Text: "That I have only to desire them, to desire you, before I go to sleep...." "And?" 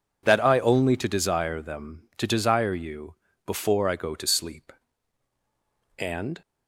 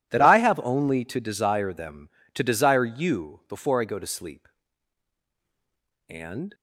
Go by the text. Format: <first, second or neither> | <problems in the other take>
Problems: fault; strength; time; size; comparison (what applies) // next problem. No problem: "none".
second | skips "have"; at 0.5 s